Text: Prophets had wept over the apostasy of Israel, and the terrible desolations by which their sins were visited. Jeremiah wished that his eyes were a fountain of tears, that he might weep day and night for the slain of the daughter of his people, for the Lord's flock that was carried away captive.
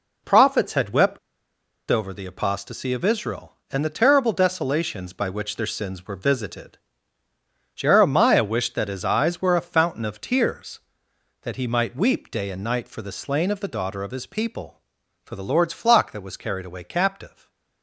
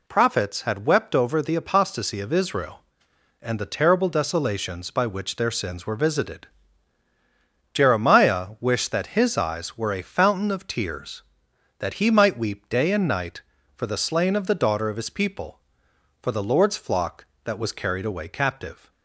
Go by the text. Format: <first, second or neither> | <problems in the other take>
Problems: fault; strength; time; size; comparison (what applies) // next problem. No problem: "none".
second | pauses between "wept" and "over"; noticeable; at 1.1 s; 0.71 s long // stays silent after the last word; slight; from 17.2 s on; 0.6 s long